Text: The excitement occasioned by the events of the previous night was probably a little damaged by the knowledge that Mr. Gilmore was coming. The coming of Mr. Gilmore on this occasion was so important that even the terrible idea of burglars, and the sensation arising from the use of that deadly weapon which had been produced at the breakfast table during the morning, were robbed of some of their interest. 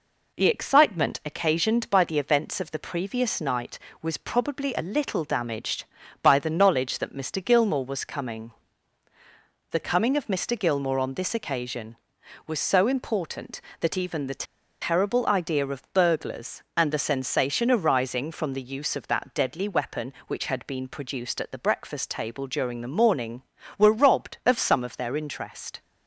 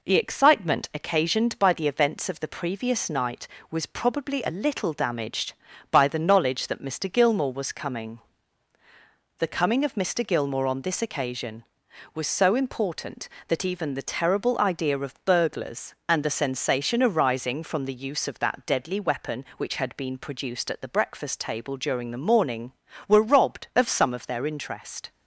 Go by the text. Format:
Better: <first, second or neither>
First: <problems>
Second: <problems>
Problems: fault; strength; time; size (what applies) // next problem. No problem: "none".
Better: second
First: pauses between "the" and "terrible"; at 14.4 s; 0.38 s long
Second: none